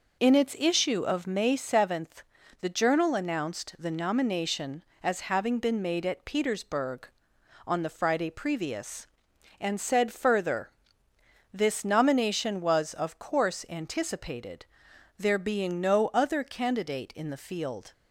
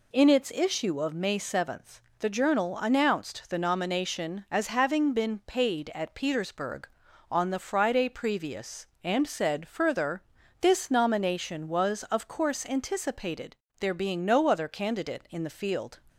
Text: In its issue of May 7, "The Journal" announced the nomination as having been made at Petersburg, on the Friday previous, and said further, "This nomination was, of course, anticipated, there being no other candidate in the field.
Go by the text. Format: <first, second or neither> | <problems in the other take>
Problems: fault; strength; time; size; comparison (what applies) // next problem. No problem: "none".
first | says "paid" for "made"; at 5.4 s